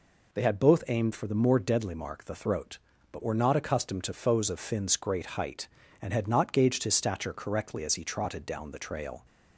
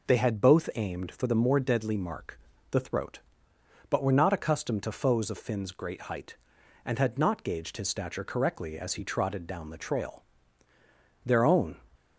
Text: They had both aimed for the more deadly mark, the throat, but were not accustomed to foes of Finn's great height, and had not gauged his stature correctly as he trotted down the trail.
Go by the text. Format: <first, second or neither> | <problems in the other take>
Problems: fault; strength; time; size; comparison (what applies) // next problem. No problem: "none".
first | goes on to say "Their own"; from 11.2 s on; 0.52 s long